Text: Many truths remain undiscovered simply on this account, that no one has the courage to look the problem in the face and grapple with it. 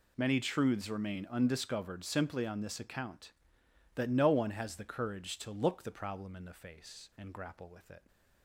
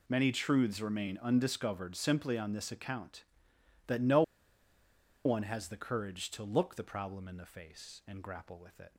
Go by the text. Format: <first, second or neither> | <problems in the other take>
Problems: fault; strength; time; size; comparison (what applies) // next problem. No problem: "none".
first | pauses between "no" and "one"; at 4.2 s; 1.0 s long